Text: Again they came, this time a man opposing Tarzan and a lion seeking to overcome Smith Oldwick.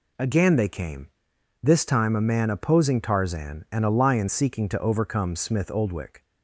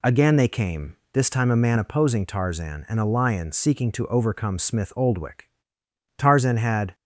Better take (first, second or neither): first